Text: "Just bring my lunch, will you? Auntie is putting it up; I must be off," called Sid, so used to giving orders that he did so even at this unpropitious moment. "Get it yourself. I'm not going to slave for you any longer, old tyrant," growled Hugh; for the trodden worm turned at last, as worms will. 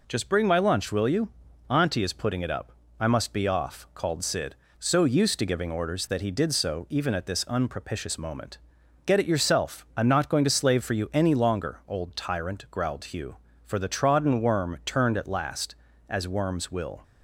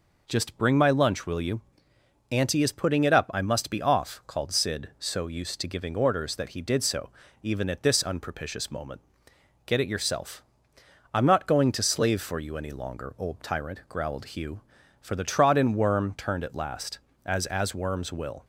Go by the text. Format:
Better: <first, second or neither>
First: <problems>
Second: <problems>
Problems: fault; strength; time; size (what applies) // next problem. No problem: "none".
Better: first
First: none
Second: pauses between "so" and "even"; slight; at 7.0 s; 0.32 s long // says "as" twice; at 17.4 s